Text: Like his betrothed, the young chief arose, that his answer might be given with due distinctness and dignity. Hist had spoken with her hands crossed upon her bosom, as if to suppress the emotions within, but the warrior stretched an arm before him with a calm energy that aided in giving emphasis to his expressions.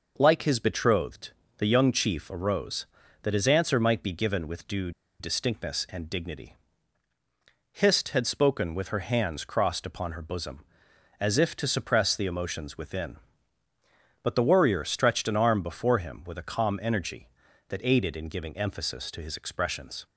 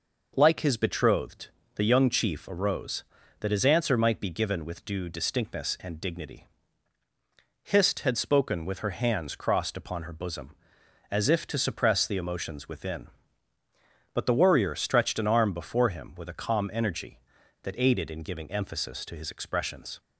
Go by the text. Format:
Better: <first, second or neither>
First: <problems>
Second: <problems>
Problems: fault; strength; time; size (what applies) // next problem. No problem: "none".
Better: second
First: pauses between "due" and "distinctness"; slight; at 4.9 s; 0.29 s long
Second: none